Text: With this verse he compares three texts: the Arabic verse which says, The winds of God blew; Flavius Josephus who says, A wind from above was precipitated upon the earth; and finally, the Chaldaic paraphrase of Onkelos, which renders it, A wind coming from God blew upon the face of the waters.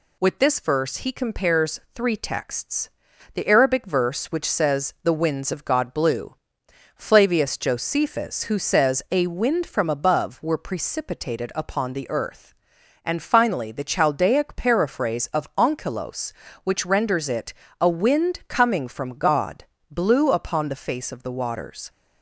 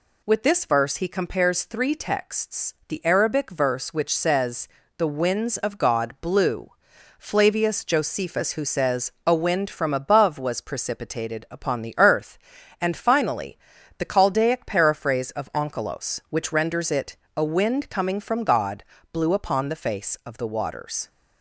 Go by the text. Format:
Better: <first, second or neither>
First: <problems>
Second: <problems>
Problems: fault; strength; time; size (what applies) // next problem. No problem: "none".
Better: second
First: pauses between "compares" and "three"; slight; at 1.7 s; 0.16 s long // says "were" for "was"; at 10.3 s // pauses between "God" and "blew"; slight; at 19.6 s; 0.26 s long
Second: pauses between "God" and "blew"; slight; at 18.8 s; 0.26 s long